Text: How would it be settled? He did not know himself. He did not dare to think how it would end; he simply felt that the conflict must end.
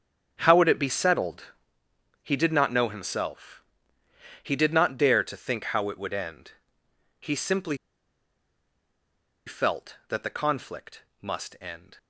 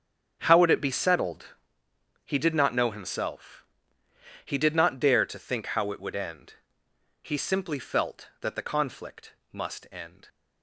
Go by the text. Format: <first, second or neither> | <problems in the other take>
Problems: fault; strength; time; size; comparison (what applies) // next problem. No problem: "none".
second | starts louder than the rest; strong; until 1.4 s; 7.5 dB; strong in the second // pauses between "simply" and "felt"; strong; at 7.7 s; 1.7 s long // pauses between "conflict" and "must"; slight; at 11.0 s; 0.18 s long; slight in the second